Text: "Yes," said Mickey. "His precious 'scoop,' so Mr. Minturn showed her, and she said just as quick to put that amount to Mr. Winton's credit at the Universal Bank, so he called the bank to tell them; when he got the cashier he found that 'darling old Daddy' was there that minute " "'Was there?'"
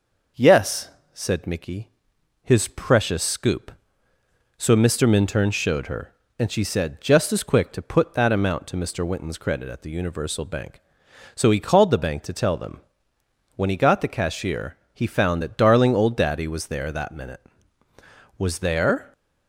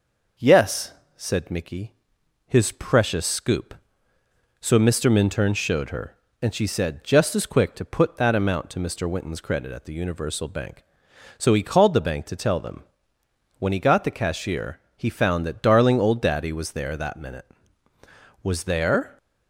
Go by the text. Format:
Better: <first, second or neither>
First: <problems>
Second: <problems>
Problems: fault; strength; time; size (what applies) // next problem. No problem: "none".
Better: neither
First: pauses between "cashier" and "he"; slight; at 14.7 s; 0.16 s long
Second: pauses between "cashier" and "he"; slight; at 14.7 s; 0.16 s long